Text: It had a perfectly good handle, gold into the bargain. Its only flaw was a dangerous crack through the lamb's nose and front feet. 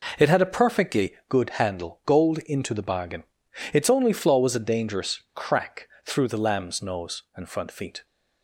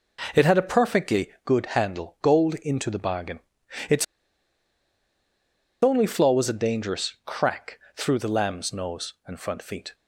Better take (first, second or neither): first